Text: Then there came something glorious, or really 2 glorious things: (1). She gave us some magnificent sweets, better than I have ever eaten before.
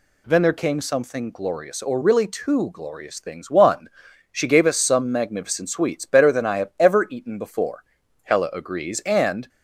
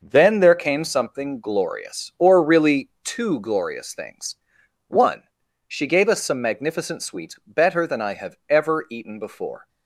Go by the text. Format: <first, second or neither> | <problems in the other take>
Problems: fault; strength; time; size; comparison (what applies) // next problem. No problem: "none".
second | goes on to say "Hella agrees and"; noticeable; from 8.2 s on; 1.2 s long